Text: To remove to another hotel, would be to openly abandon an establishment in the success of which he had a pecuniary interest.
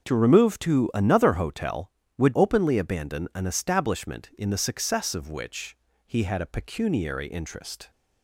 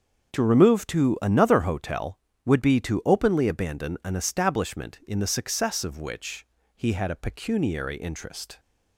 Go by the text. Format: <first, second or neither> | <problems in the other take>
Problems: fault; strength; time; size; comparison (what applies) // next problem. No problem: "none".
second | starts louder than the rest; until 1.1 s; 6.5 dB; also in the second // skips "be to"; at 2.3 s // pauses between "which" and "he"; slight; at 5.7 s; 0.30 s long; slight in the second